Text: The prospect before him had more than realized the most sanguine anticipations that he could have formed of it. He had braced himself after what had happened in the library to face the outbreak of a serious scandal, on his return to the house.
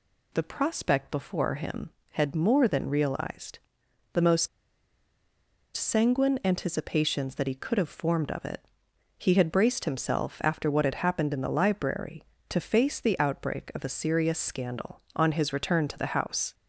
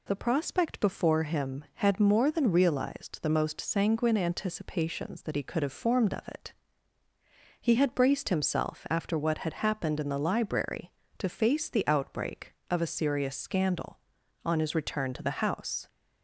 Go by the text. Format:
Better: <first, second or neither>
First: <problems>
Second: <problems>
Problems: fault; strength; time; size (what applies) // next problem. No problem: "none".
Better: second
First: pauses between "realized" and "the"; noticeable; at 3.5 s; 0.56 s long // pauses between "most" and "sanguine"; strong; at 4.4 s; 1.2 s long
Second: none